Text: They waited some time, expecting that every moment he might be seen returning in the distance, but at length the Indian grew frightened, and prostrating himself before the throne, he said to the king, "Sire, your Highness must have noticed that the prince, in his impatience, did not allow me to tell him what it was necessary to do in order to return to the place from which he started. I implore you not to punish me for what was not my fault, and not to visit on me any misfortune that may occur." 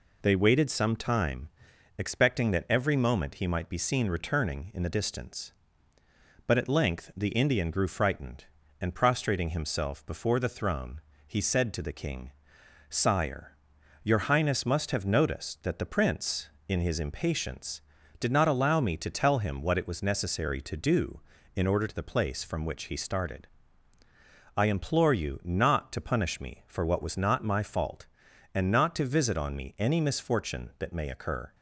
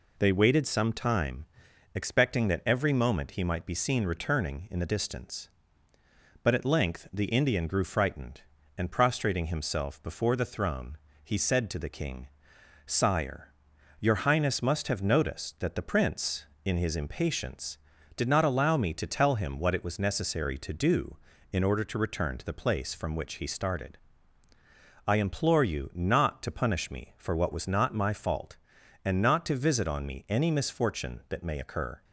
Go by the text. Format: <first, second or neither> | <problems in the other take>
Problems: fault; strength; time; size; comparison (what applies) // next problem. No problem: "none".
second | skips "to return"; at 21.8 s